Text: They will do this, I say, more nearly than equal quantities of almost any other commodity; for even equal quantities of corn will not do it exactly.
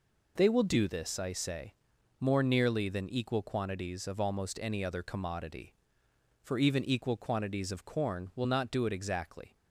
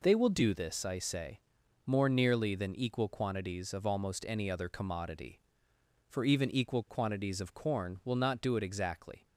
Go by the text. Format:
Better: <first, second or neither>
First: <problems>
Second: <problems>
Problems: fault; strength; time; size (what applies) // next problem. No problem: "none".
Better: neither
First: none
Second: none